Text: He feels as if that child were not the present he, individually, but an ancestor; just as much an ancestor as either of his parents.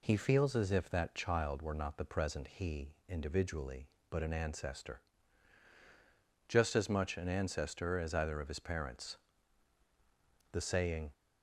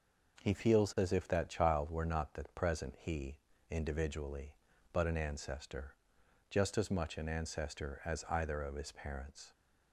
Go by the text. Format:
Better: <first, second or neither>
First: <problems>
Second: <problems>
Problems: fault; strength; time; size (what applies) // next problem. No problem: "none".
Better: second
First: goes on to say "The saying"; noticeable; from 10.5 s on; 0.62 s long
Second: none